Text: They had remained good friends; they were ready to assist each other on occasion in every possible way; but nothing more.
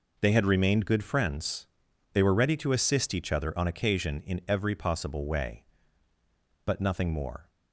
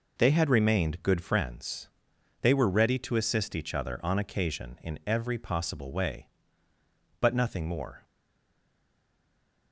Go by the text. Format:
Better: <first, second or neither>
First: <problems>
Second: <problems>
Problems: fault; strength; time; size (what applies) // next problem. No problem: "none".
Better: first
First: none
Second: stays silent after the last word; noticeable; from 8.0 s on; 1.7 s long